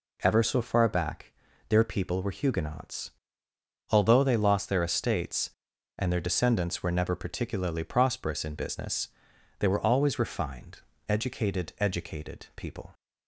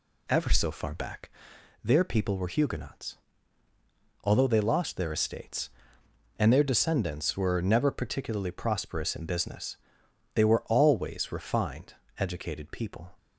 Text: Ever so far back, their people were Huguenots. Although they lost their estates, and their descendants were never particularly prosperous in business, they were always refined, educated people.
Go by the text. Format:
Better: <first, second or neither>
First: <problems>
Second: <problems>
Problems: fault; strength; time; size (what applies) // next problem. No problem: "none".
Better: second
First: says "educated" twice; at 11.7 s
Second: none